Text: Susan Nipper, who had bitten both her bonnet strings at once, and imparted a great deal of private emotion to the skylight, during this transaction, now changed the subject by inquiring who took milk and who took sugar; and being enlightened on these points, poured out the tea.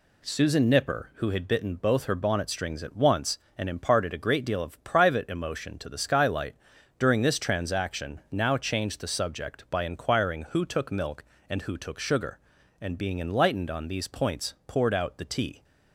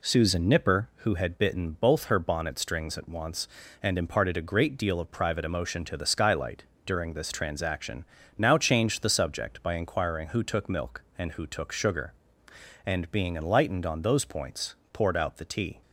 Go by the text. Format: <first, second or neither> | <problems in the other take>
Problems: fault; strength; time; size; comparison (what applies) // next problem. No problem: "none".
first | says "those" for "these"; at 14.0 s